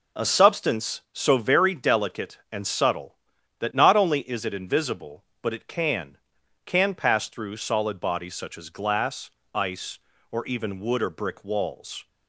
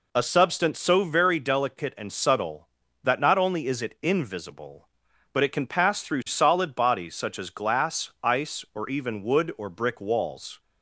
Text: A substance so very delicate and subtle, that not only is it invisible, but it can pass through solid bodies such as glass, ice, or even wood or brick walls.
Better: second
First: says "can" twice; at 6.6 s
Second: none

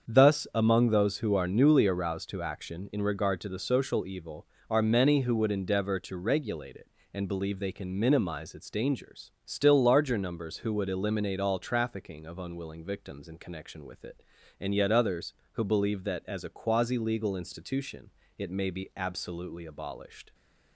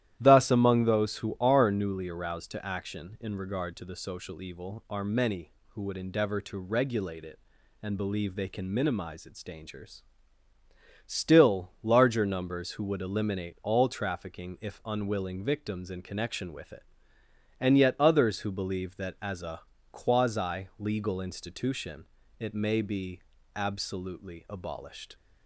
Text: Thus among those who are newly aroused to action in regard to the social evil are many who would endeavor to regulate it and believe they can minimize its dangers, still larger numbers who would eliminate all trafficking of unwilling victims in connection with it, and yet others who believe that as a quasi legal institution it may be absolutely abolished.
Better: first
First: starts louder than the rest; until 1.1 s; 7 dB // pauses between "institution" and "it"; slight; at 18.0 s; 0.26 s long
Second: starts louder than the rest; strong; until 1.2 s; 12.5 dB // says "if" for "of"; at 14.6 s // pauses between "a" and "quasi"; slight; at 19.6 s; 0.30 s long // pauses between "institution" and "it"; slight; at 22.0 s; 0.34 s long // pauses between "be" and "absolutely"; slight; at 23.1 s; 0.36 s long

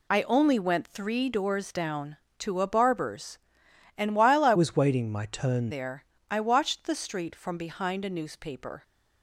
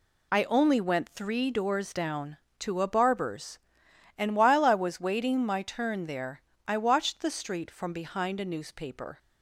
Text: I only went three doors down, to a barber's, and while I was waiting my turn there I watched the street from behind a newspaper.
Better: second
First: changes voice from "was" to "turn"; from 4.5 to 5.6 s; 1.1 s long // pauses between "there" and "I"; slight; at 6.0 s; 0.26 s long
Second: pauses between "there" and "I"; slight; at 6.3 s; 0.26 s long

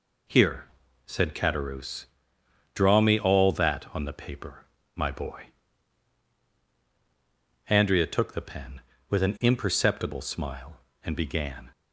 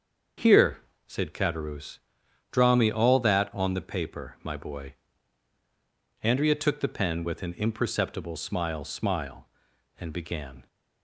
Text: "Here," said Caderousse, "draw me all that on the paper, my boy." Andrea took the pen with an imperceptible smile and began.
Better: first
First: none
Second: starts louder than the rest; until 1.6 s; 7 dB // says "smile" twice; at 8.8 s

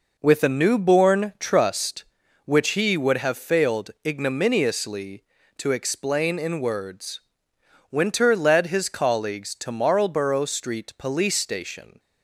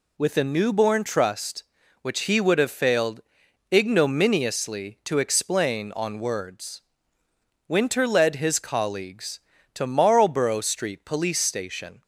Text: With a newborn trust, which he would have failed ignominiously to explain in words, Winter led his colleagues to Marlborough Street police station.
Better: first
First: none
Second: pauses between "failed" and "ignominiously"; noticeable; at 3.2 s; 0.52 s long // says "on" for "in"; at 5.9 s

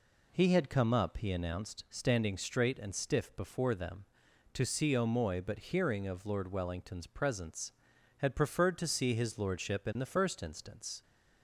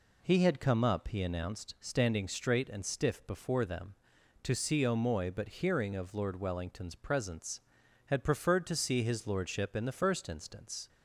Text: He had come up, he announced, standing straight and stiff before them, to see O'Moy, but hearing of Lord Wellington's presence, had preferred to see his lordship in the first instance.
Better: neither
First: none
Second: none

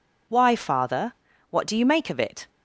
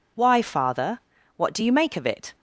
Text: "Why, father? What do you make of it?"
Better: neither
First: none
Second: none

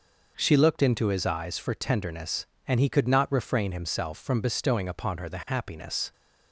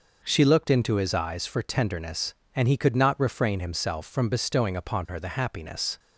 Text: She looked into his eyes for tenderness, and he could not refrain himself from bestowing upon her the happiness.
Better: neither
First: none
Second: none

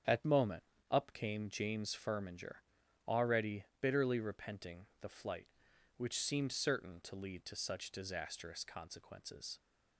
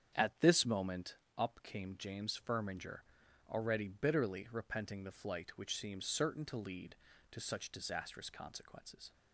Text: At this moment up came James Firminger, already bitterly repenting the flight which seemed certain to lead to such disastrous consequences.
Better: second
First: starts louder than the rest; strong; until 1.3 s; 8.5 dB // skips "this"; at 0.2 s // pauses between "moment" and "up"; slight; at 0.6 s; 0.28 s long // pauses between "already" and "bitterly"; slight; at 3.6 s; 0.16 s long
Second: starts louder than the rest; strong; until 1.4 s; 8 dB // pauses between "moment" and "up"; slight; at 1.1 s; 0.22 s long

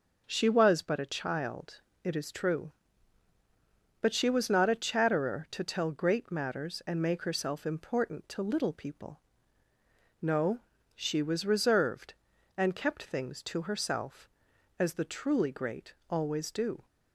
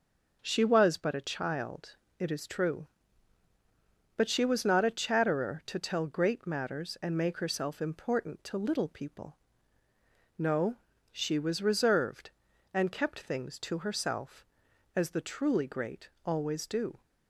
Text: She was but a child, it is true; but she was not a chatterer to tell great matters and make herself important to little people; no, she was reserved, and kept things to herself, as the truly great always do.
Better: neither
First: pauses between "great" and "always"; slight; at 15.9 s; 0.16 s long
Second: pauses between "great" and "always"; slight; at 16.0 s; 0.16 s long

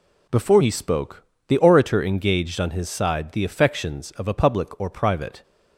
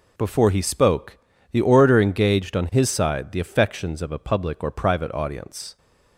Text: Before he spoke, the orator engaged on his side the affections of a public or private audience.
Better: second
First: stops before "audience"; at 5.4 s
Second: none

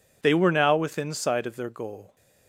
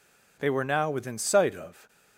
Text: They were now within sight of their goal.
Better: first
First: none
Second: stops before "their goal"; at 1.8 s

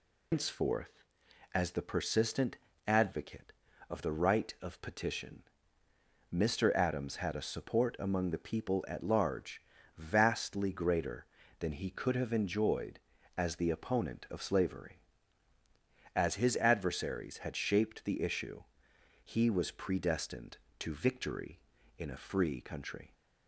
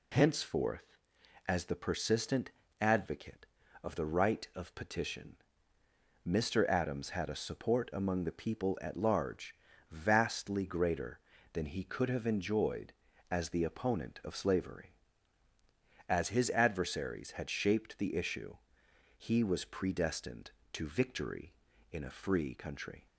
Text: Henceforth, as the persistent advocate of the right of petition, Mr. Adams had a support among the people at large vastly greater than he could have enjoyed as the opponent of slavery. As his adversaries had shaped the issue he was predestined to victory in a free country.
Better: second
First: loses the start of "Henceforth"; at 0.3 s; 140 ms // pauses between "persistent" and "advocate"; slight; at 2.5 s; 0.28 s long // pauses between "large" and "vastly"; slight; at 9.6 s; 0.36 s long // pauses between "issue" and "he"; noticeable; at 18.6 s; 0.60 s long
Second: pauses between "persistent" and "advocate"; slight; at 2.5 s; 0.28 s long // pauses between "large" and "vastly"; slight; at 9.5 s; 0.36 s long // pauses between "issue" and "he"; noticeable; at 18.5 s; 0.60 s long

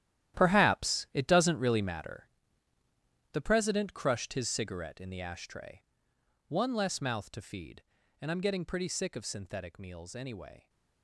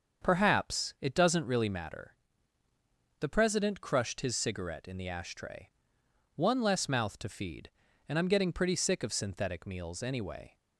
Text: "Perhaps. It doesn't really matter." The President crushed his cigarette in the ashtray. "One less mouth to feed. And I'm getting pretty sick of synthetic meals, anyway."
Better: second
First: gets quieter; strong; throughout; 13 dB // starts louder than the rest; strong; until 1.4 s; 12 dB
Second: starts louder than the rest; until 1.2 s; 7 dB

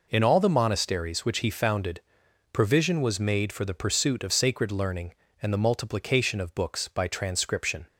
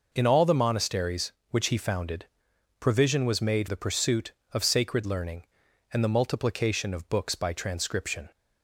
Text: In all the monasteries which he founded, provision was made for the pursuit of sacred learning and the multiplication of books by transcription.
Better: first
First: none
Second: skips "for"; at 3.6 s

